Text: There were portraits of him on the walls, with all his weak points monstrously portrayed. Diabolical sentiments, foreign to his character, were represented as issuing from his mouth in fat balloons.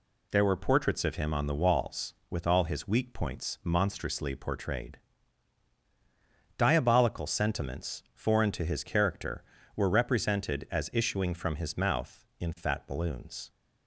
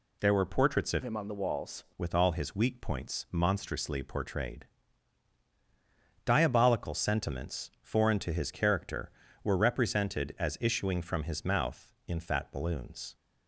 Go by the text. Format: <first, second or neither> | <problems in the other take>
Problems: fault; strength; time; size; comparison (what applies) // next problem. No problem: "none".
first | changes voice from "him" to "walls"; from 1.0 to 1.8 s; 0.8 s long